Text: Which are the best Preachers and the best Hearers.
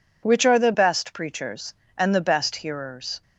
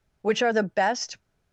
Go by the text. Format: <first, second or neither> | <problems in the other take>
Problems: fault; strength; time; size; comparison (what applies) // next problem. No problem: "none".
first | stops before "Preachers and the best Hearers"; at 1.2 s